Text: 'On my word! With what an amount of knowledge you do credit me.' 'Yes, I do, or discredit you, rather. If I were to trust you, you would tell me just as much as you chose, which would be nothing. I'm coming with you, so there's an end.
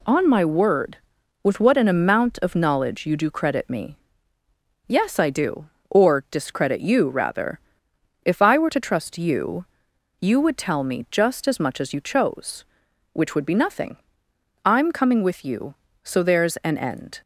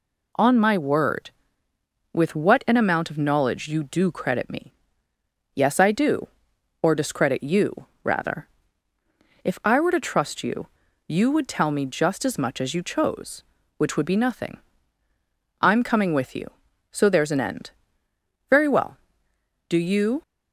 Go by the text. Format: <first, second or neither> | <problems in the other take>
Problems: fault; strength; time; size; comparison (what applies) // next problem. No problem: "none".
first | goes on to say "Very well Do you"; strong; from 18.4 s on; 1.7 s long